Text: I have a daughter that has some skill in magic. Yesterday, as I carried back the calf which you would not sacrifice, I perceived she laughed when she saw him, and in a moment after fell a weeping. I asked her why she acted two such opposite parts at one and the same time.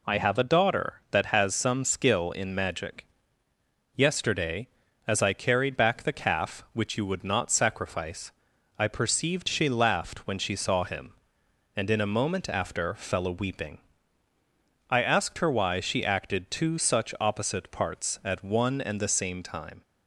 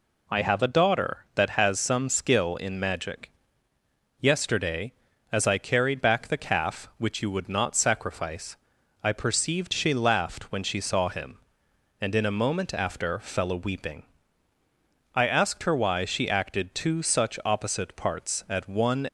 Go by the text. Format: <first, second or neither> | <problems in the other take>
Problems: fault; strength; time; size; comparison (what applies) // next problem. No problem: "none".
first | stops before "and the same time"; at 19.0 s